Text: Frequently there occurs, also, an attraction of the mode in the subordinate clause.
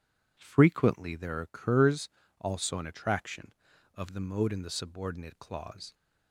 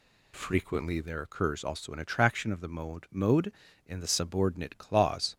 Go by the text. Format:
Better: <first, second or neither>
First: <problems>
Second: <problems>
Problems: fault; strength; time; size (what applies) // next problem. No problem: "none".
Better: first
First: none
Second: says "mode" twice; at 3.0 s